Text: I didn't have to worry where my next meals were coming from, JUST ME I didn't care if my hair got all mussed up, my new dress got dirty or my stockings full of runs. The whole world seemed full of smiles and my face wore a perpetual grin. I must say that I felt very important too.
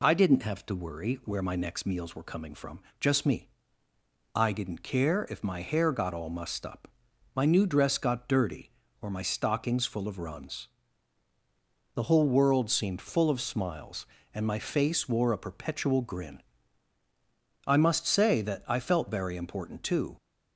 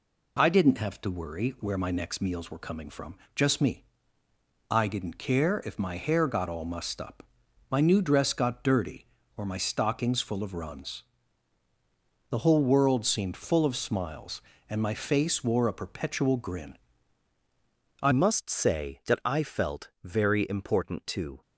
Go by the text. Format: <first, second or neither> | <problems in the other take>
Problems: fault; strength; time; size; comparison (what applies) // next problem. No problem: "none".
first | pauses between "ME" and "I"; noticeable; at 3.8 s; 0.88 s long; noticeable in the first // changes voice at "must"; from 18.1 s on; 3.3 s long